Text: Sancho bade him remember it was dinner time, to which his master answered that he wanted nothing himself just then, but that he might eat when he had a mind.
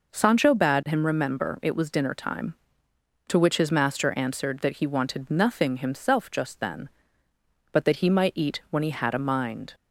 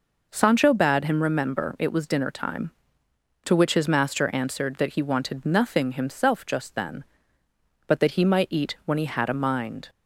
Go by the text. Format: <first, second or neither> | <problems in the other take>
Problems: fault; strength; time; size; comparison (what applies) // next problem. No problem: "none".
neither | none